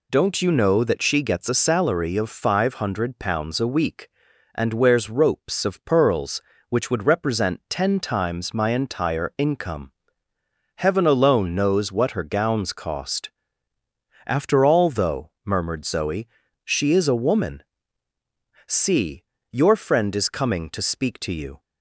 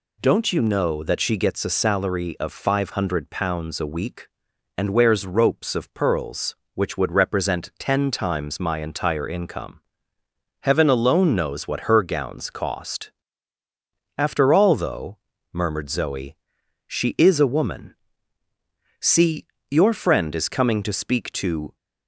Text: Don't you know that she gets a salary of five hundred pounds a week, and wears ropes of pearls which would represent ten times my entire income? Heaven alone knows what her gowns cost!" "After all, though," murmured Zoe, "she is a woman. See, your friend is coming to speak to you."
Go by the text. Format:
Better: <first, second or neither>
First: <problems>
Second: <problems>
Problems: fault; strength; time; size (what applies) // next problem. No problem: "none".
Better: first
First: none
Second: stops before "you"; at 21.7 s